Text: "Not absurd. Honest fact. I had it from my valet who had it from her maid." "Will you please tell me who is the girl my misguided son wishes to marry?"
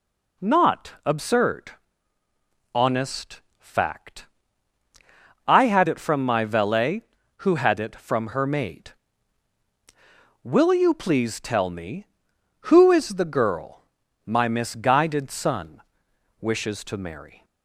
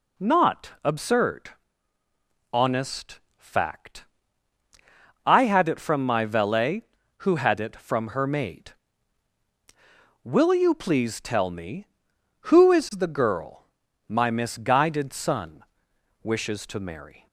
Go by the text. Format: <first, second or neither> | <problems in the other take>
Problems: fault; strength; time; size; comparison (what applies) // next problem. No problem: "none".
neither | pauses between "Honest" and "fact"; slight; the same in both // pauses between "girl" and "my"; the same in both // pauses between "son" and "wishes"; noticeable; the same in both